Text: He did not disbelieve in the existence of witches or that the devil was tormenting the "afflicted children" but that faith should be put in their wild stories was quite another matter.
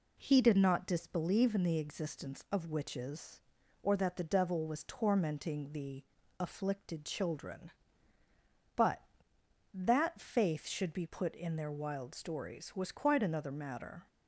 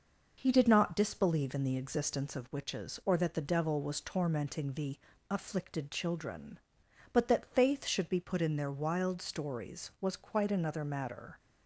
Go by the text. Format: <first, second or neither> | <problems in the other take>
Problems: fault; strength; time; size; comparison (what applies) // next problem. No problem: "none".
neither | pauses between "the" and "afflicted"; slight; the same in both